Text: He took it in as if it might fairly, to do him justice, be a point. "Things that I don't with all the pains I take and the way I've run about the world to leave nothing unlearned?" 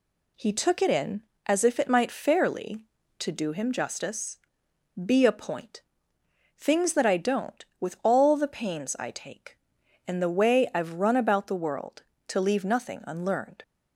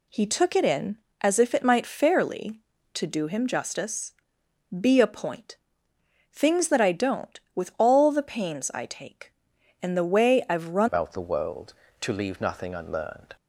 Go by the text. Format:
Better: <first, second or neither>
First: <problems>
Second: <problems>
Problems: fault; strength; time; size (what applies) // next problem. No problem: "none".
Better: first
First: none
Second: changes voice at "about"; from 10.8 s on; 2.5 s long